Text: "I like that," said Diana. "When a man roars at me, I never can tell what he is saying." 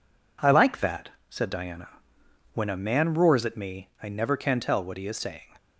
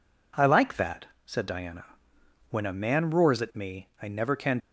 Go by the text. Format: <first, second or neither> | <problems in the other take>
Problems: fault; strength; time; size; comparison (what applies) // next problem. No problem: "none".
first | stops before "tell what he is saying"; at 4.6 s